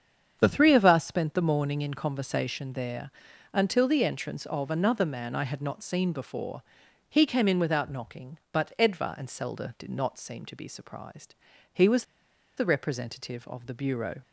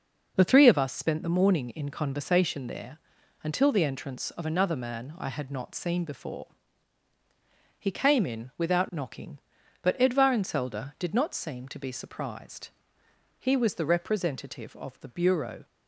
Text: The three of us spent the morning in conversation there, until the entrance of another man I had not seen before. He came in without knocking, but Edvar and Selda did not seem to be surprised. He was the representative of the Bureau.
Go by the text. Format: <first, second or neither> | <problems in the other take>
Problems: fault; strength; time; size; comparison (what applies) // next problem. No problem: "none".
second | starts louder than the rest; strong; until 1.4 s; 7.5 dB // pauses between "was" and "the"; noticeable; at 12.0 s; 0.53 s long